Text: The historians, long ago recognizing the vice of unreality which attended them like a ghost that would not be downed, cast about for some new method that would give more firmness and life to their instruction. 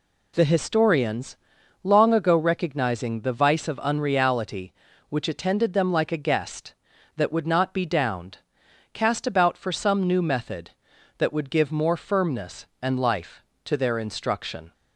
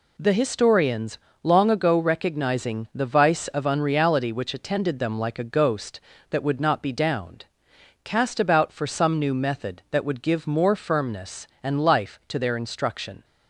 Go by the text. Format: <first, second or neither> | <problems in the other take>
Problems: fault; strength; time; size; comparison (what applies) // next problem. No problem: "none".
second | says "guest" for "ghost"; at 6.2 s